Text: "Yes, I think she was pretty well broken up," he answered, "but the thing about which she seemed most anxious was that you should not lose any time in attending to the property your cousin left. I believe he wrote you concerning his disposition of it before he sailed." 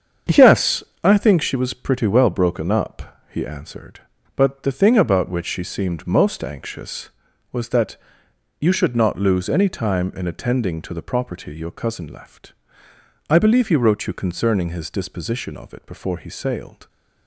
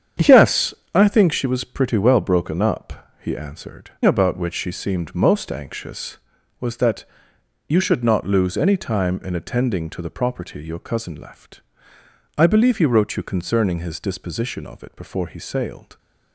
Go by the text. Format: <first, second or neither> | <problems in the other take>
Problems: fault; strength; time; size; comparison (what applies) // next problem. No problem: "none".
first | starts louder than the rest; strong; until 1.3 s; 8.5 dB; strong in the first // skips "but the thing"; at 3.9 s // pauses between "that" and "you"; noticeable; at 7.0 s; 0.64 s long; noticeable in the first